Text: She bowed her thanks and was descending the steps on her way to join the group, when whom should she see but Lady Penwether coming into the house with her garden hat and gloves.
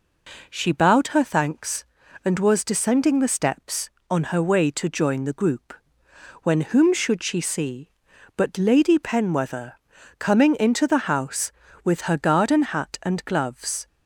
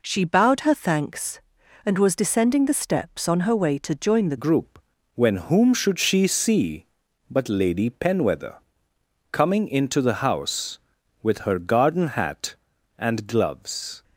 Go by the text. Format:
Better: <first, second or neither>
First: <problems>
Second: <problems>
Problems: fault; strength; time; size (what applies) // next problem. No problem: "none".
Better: first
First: pauses between "Penwether" and "coming"; noticeable; at 9.7 s; 0.46 s long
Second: changes voice at "group"; from 4.3 s on; 9.7 s long // pauses between "Penwether" and "coming"; noticeable; at 8.5 s; 0.76 s long